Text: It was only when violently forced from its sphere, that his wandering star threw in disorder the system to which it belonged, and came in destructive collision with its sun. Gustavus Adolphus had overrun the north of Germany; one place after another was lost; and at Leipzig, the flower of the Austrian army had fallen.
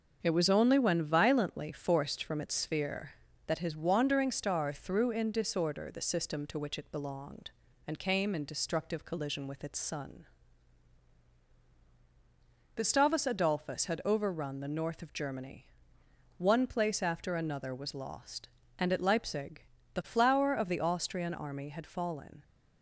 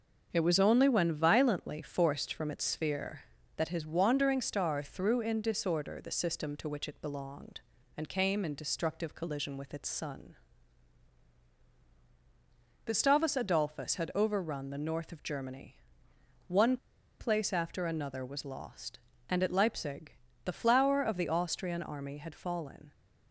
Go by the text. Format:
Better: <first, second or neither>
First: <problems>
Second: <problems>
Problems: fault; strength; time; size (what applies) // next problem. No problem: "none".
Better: first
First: starts louder than the rest; until 1.2 s; 6.5 dB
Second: starts louder than the rest; until 1.3 s; 6.5 dB // pauses between "one" and "place"; at 16.7 s; 0.43 s long